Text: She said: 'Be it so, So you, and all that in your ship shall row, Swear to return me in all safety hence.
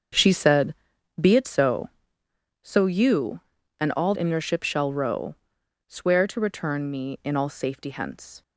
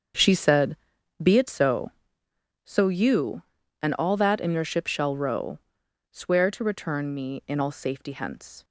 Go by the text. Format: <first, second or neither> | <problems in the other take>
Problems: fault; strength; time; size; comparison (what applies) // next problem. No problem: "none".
second | starts louder than the rest; until 1.5 s; 7 dB; also in the second // skips "that"; at 4.1 s